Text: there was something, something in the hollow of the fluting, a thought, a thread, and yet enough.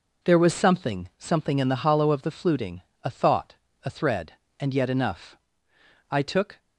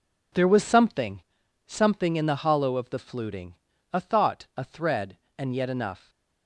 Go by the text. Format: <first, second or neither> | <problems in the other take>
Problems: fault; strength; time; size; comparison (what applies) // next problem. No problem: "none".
second | goes on to say "I took"; from 6.1 s on; 0.50 s long